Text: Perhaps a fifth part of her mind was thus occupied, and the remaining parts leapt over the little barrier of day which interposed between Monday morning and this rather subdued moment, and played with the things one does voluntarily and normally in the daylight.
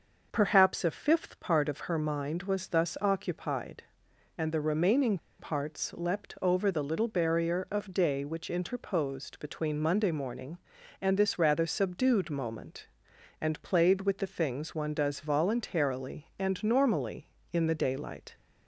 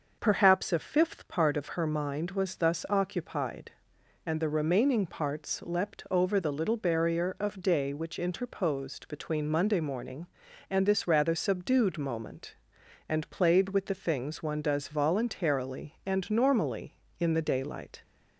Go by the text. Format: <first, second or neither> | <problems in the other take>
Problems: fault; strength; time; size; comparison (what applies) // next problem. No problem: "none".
second | starts louder than the rest; noticeable; until 1.3 s; 6 dB; noticeable in the second // pauses between "remaining" and "parts"; slight; at 5.1 s; 0.21 s long